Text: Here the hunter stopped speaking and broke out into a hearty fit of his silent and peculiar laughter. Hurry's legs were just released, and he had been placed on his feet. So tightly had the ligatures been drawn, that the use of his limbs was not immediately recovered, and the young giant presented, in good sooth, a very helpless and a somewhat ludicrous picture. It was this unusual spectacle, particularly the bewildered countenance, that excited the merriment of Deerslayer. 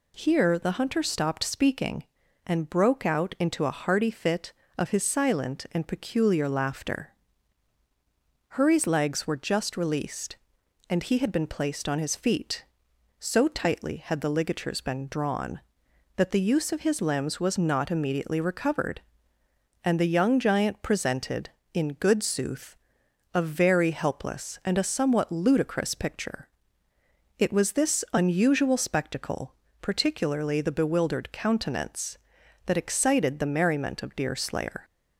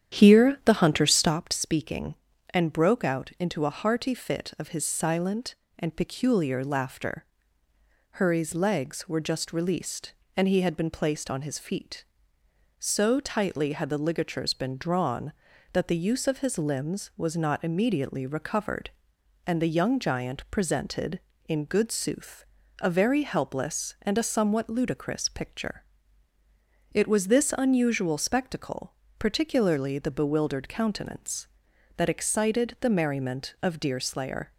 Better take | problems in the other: first | starts louder than the rest; strong; until 1.4 s; 9.5 dB

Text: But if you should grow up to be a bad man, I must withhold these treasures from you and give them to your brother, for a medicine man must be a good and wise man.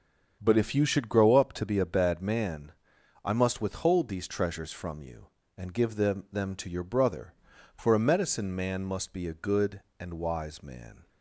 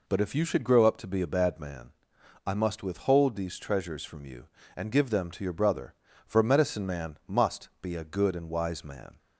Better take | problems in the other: second | starts louder than the rest; until 1.4 s; 7 dB // says "them" twice; at 6.3 s

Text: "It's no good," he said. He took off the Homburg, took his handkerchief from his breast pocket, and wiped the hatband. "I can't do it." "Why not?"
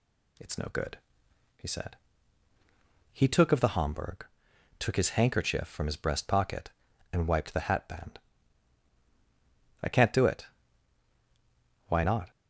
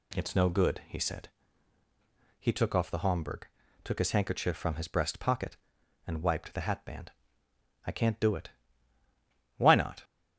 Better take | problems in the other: second | says "of" for "off"; at 3.5 s

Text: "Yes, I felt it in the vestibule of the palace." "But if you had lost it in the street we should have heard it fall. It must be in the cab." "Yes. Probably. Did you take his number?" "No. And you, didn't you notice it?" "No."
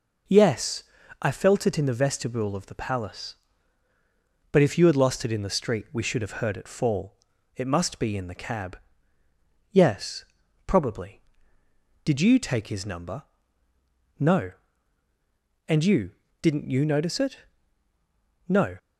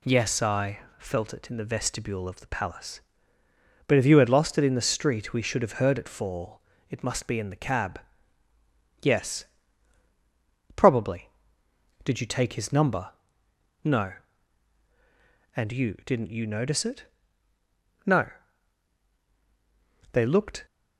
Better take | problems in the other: first | pauses between "I" and "felt"; slight; at 0.7 s; 0.18 s long // goes on to say "They looked"; from 20.1 s on; 0.54 s long

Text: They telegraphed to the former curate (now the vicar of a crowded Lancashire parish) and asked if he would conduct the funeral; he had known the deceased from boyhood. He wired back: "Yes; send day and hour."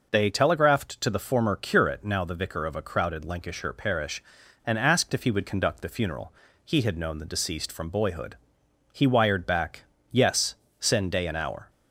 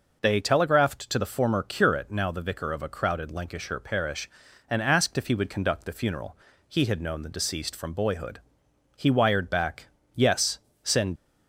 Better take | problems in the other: first | stops before "day and hour"; at 11.1 s

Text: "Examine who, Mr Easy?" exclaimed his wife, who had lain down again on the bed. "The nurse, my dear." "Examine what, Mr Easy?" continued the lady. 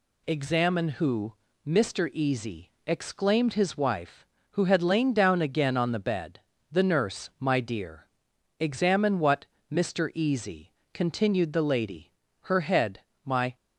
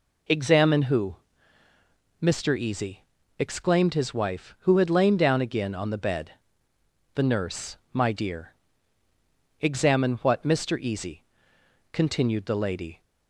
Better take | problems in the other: second | goes on to say "Her head my"; noticeable; from 12.4 s on; 1.1 s long

